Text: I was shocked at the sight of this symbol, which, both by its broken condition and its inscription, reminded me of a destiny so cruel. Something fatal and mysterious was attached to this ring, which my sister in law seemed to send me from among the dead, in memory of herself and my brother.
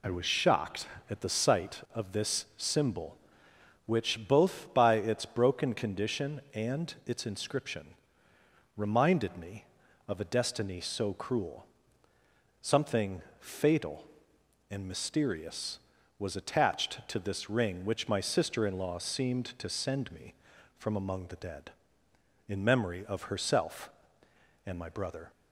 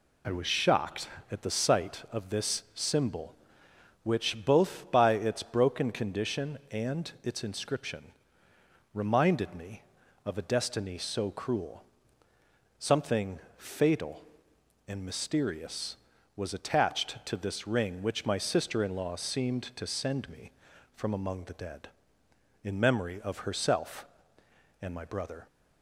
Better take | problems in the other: neither | pauses between "Something" and "fatal"; slight; the same in both

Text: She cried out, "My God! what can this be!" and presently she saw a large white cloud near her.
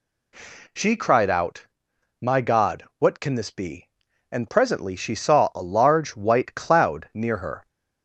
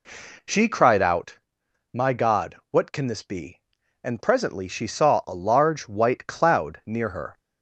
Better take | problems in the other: first | starts louder than the rest; slight; until 1.3 s; 3 dB

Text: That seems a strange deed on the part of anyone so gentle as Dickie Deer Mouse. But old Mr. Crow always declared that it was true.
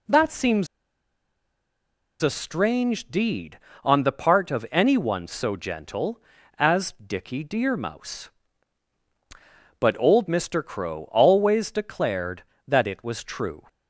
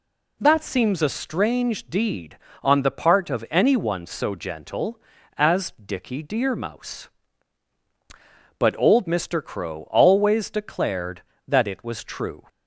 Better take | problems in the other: second | pauses between "seems" and "a"; strong; at 0.6 s; 1.5 s long

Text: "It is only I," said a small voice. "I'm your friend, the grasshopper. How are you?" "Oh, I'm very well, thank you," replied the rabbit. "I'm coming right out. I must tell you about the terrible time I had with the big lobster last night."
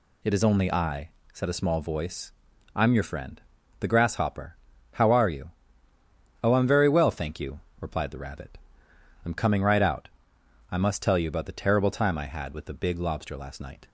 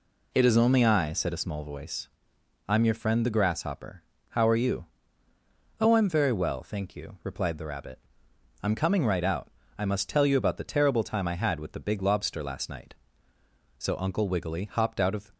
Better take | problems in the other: first | goes on to say "So Uncle Wiggily hopped out of"; from 13.7 s on; 1.5 s long

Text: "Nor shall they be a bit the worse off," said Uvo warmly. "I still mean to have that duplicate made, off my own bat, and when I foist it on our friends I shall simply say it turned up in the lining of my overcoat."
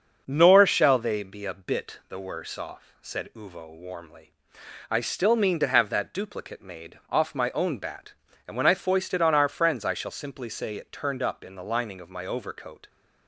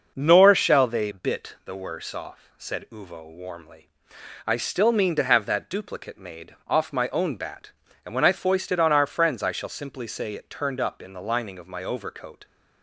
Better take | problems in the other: first | starts louder than the rest; noticeable; until 1.1 s; 6 dB; also in the first // skips "be a"; at 1.1 s

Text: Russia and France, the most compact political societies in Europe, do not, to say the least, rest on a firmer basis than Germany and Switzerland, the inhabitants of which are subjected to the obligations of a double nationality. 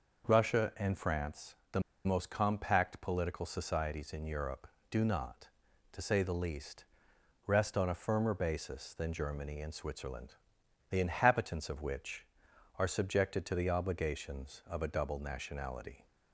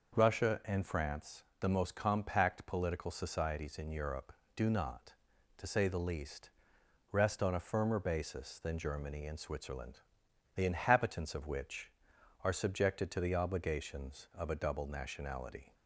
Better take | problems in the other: second | pauses between "the" and "most"; slight; at 1.7 s; 0.25 s long

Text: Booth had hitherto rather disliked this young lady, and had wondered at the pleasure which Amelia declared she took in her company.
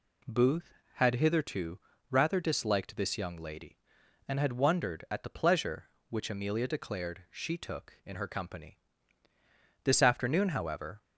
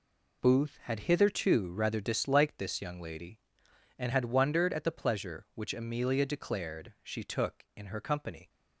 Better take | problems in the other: second | pauses between "hitherto" and "rather"; slight; at 1.7 s; 0.30 s long // goes on to say "This afternoon however"; noticeable; from 9.8 s on; 1.1 s long

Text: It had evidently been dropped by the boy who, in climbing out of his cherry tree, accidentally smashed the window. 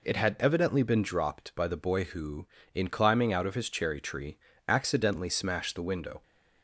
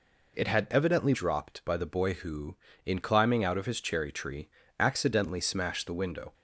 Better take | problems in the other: first | skips "been"; at 1.1 s

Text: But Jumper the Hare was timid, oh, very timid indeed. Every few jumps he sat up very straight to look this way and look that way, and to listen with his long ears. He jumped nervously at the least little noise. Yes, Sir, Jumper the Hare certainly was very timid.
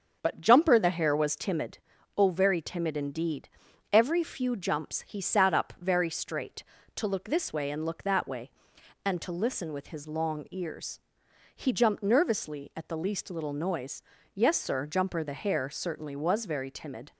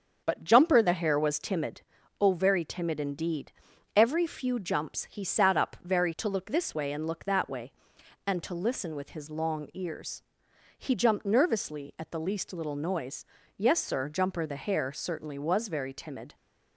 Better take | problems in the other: first | starts louder than the rest; until 1.2 s; 7 dB; also in the first // skips "straight"; at 6.1 s

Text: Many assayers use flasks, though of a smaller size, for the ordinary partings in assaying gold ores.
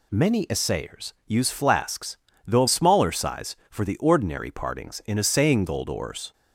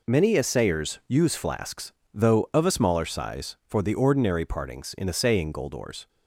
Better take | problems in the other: second | skips "a"; at 2.6 s

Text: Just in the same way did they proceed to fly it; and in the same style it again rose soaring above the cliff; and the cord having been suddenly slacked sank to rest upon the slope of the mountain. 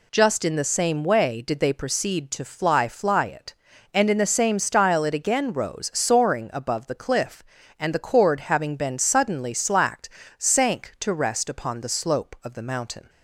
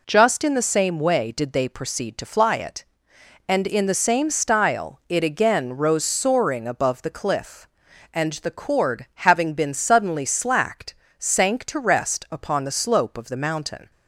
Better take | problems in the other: second | says "fly" twice; at 2.8 s // pauses between "slacked" and "sank"; slight; at 10.0 s; 0.30 s long; slight in the second

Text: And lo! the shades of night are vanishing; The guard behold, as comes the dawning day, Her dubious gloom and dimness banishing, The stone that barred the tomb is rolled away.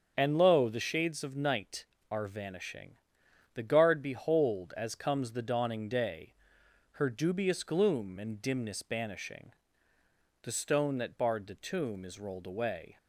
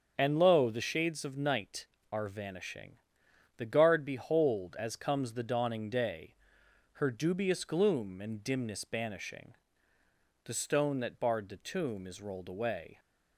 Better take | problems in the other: neither | starts louder than the rest; the same in both

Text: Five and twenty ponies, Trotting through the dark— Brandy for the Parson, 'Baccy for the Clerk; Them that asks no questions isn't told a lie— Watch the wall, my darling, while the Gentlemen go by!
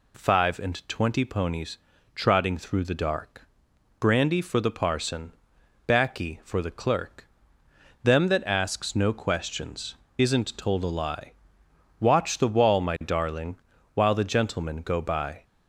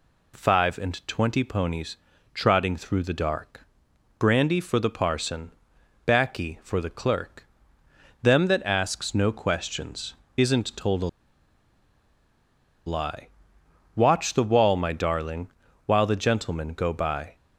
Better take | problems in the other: first | pauses between "questions" and "isn't"; slight; at 10.1 s; 0.22 s long; slight in the first // pauses between "a" and "lie"; strong; at 11.0 s; 1.7 s long

